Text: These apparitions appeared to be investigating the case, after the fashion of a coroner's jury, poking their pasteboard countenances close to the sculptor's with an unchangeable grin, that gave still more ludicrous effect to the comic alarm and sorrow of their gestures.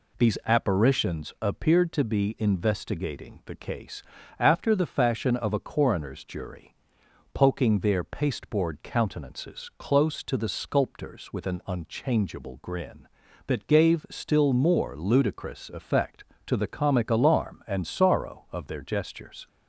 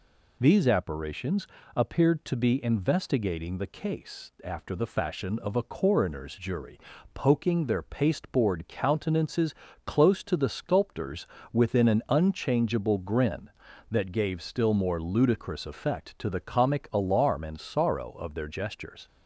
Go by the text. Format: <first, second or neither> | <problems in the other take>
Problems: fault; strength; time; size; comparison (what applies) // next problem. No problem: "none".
first | pauses between "apparitions" and "appeared"; slight; at 1.4 s; 0.30 s long // pauses between "countenances" and "close"; slight; at 9.5 s; 0.32 s long // says "within" for "with"; at 11.5 s